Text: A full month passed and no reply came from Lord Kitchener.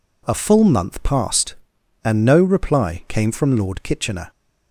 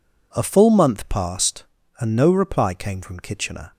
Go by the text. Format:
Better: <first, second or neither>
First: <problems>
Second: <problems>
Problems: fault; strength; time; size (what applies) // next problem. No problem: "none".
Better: first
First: none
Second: skips "Lord"; at 3.1 s